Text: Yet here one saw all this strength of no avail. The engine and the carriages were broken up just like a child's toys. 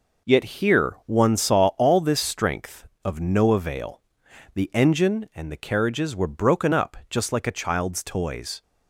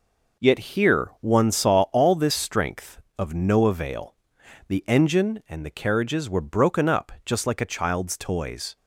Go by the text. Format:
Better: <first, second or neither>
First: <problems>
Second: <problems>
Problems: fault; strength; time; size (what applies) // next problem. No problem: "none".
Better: neither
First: none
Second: none